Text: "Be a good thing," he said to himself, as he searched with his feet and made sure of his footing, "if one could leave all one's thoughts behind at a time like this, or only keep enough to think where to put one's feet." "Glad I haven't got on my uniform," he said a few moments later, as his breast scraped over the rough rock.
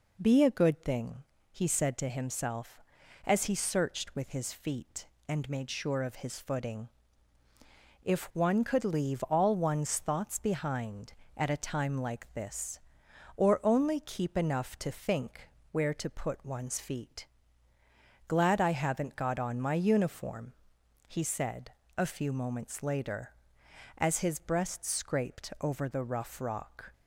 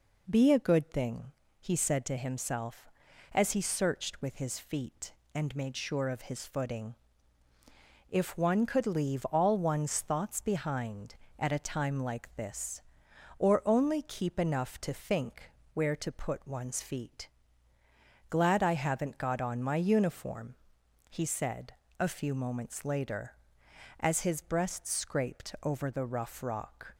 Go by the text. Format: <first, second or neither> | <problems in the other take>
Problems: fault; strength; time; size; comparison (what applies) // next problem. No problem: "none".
neither | pauses between "think" and "where"; slight; the same in both // pauses between "said" and "a"; slight; the same in both